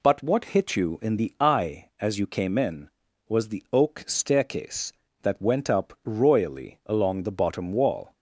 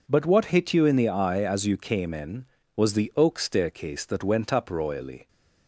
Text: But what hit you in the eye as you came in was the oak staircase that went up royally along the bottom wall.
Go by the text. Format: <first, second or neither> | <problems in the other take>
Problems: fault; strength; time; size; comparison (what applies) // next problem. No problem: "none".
first | stops before "along the bottom wall"; at 5.2 s